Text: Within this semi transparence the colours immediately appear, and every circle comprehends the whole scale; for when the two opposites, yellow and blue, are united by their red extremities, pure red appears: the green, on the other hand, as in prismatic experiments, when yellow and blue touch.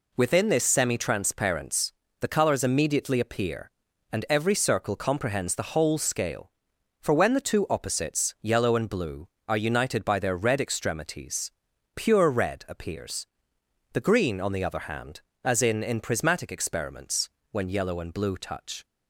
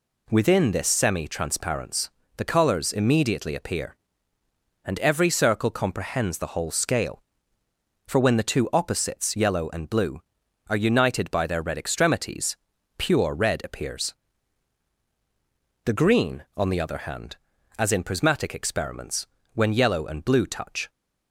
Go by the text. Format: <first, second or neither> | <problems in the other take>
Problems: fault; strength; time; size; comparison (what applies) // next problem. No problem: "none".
second | pauses between "transparence" and "the"; slight; at 1.9 s; 0.28 s long; slight in the second // says "in" twice; at 15.8 s